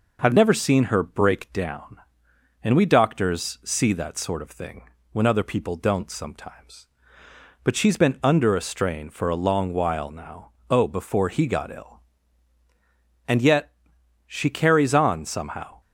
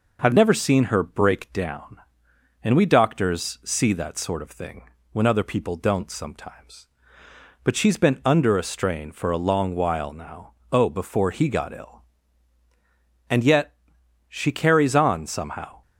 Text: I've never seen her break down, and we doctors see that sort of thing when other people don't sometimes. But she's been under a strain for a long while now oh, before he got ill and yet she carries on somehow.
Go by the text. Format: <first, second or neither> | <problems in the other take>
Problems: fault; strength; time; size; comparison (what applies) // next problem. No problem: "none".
neither | pauses between "thing" and "when"; slight; the same in both // pauses between "now" and "oh"; slight; the same in both // pauses between "yet" and "she"; noticeable; the same in both